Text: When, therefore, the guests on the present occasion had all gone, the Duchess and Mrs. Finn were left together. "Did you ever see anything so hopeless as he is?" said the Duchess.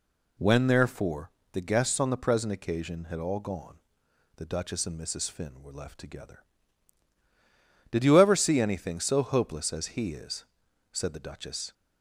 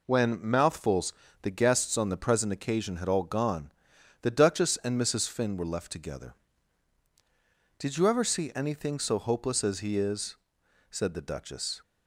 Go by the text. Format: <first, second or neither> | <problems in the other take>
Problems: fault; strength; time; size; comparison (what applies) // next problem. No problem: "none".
first | says "mouthfuls" for "therefore"; at 0.4 s